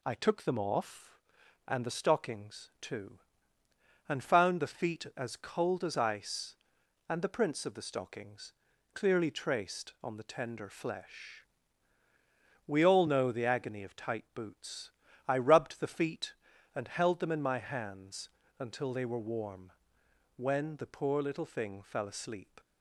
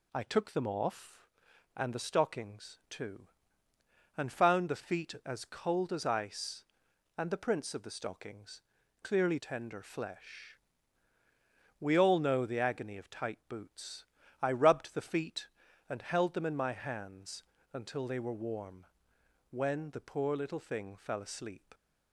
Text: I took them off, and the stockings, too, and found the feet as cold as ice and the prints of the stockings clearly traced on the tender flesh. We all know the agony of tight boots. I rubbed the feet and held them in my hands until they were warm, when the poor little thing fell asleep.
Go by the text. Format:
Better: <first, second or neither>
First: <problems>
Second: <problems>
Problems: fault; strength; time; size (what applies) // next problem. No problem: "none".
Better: first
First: pauses between "stockings" and "clearly"; at 8.5 s; 0.42 s long // pauses between "hands" and "until"; slight; at 18.2 s; 0.28 s long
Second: pauses between "stockings" and "clearly"; at 8.6 s; 0.42 s long // skips "traced on the"; at 9.3 s // pauses between "hands" and "until"; slight; at 17.4 s; 0.28 s long